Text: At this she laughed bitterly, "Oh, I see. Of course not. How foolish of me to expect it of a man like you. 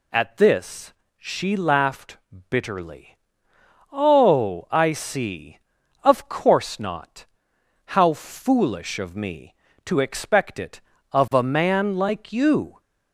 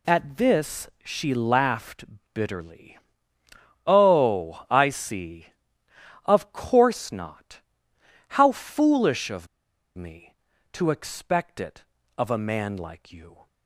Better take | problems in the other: first | pauses between "this" and "she"; slight; at 0.8 s; 0.16 s long; slight in the first // pauses between "laughed" and "bitterly"; slight; at 2.0 s; 0.28 s long; slight in the first // pauses between "of" and "me"; noticeable; at 9.4 s; 0.49 s long

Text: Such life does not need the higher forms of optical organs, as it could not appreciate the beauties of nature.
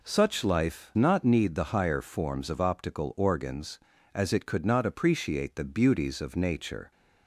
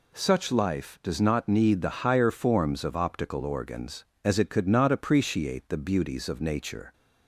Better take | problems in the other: second | skips "does"; at 0.9 s

